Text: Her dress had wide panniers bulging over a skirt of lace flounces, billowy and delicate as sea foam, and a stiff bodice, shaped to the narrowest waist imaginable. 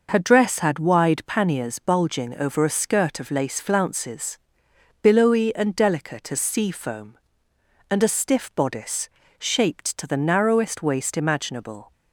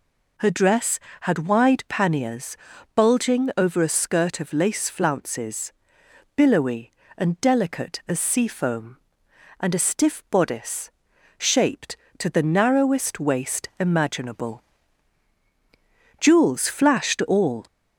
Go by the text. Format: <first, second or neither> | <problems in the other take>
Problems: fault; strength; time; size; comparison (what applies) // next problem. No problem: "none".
first | pauses between "panniers" and "bulging"; at 2.5 s; 0.38 s long // goes on to say "Jewels flashed all"; from 16.1 s on; 1.4 s long